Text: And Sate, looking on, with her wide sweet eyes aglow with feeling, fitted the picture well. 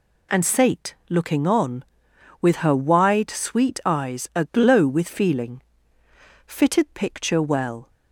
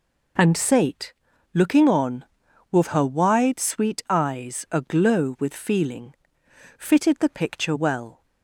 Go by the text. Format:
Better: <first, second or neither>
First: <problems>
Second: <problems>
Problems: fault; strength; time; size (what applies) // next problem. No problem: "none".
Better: second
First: skips "the"; at 6.8 s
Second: none